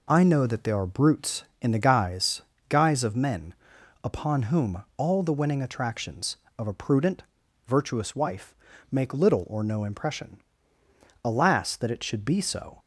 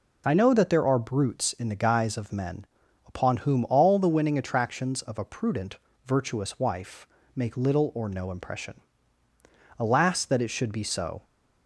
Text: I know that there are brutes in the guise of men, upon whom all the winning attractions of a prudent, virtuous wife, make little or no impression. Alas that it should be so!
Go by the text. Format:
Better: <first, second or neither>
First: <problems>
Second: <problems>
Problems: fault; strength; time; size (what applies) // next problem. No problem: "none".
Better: second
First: says "guise" twice; at 2.6 s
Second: none